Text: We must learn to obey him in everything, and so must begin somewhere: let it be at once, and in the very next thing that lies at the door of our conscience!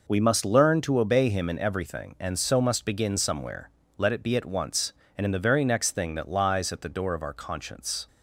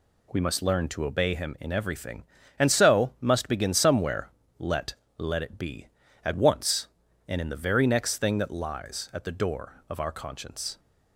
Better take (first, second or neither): first